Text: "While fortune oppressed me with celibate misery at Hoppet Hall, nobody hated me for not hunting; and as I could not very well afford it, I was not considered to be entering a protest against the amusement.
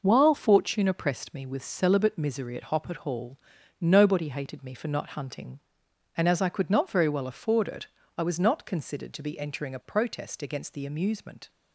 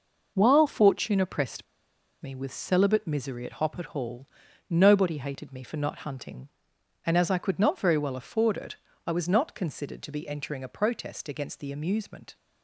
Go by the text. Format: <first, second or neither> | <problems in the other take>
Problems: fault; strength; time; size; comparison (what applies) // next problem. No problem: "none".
first | pauses between "oppressed" and "me"; noticeable; at 1.6 s; 0.57 s long